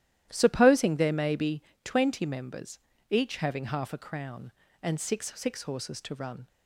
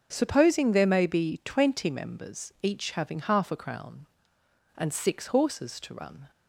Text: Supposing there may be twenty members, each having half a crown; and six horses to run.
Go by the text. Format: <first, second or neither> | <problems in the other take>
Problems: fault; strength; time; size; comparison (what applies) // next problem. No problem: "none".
second | starts louder than the rest; strong; until 1.3 s; 13 dB; noticeable in the second // pauses between "be" and "twenty"; slight; at 1.6 s; 0.22 s long // says "six" twice; at 5.3 s